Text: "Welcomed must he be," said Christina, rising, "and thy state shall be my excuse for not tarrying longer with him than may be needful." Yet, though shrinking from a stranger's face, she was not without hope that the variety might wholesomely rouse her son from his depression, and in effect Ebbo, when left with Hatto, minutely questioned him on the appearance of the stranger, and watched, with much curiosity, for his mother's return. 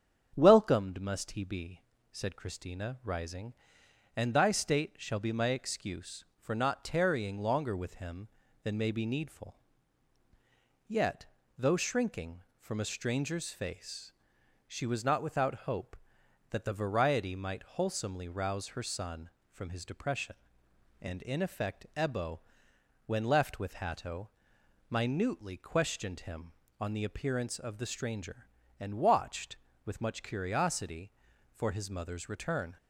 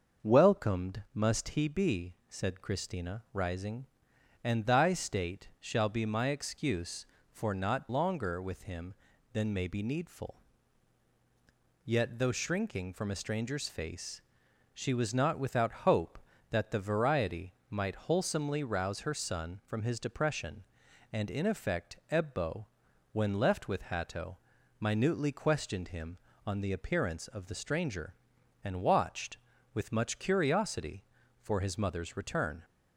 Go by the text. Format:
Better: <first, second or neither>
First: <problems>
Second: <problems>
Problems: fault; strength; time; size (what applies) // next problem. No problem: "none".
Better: first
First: starts louder than the rest; strong; until 1.3 s; 7.5 dB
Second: starts louder than the rest; until 1.3 s; 6 dB // skips "tarrying"; at 7.8 s // pauses between "variety" and "might"; slight; at 17.5 s; 0.16 s long